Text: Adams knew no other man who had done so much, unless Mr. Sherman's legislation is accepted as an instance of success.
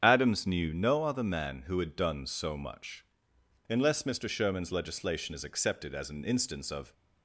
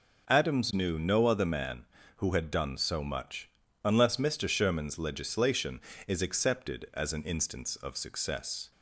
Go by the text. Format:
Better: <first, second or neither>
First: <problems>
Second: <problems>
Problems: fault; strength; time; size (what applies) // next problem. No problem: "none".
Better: second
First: starts louder than the rest; strong; until 1.0 s; 8 dB // stops before "success"; at 6.9 s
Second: none